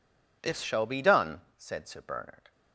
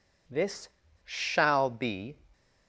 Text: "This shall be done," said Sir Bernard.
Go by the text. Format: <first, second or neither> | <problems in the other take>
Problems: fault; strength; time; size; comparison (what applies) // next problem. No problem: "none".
first | pauses between "This" and "shall"; slight; at 0.7 s; 0.33 s long // stops before "done said Sir Bernard"; at 2.3 s